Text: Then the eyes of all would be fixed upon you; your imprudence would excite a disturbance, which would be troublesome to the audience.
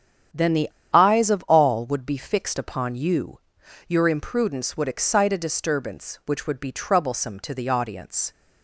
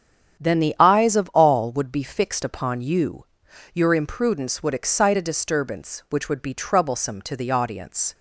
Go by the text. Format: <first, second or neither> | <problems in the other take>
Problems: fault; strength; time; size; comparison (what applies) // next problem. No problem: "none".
second | starts louder than the rest; strong; until 1.5 s; 8 dB; strong in the second // pauses between "the" and "eyes"; slight; at 0.6 s; 0.24 s long